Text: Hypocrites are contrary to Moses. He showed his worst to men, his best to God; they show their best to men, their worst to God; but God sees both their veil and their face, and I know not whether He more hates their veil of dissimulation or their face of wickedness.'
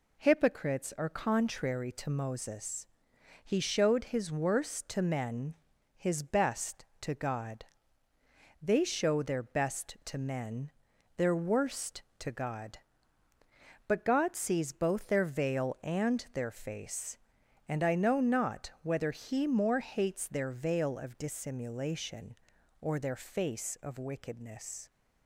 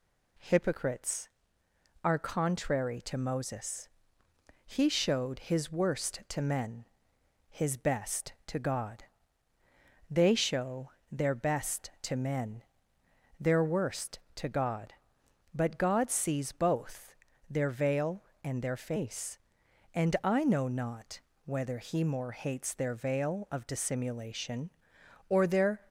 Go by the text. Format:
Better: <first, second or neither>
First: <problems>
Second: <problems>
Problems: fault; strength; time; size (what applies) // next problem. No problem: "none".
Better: first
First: none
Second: pauses between "show" and "their"; slight; at 10.8 s; 0.22 s long // pauses between "both" and "their"; slight; at 17.1 s; 0.36 s long // pauses between "not" and "whether"; slight; at 21.1 s; 0.24 s long // stops before "face of wickedness"; at 25.8 s